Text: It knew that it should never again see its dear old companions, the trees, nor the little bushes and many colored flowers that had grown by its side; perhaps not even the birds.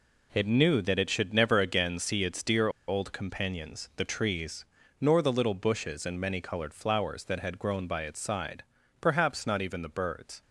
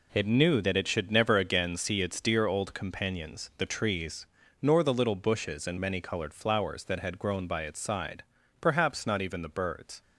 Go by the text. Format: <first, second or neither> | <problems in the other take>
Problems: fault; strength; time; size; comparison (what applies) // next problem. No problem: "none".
second | pauses between "dear" and "old"; slight; at 2.6 s; 0.19 s long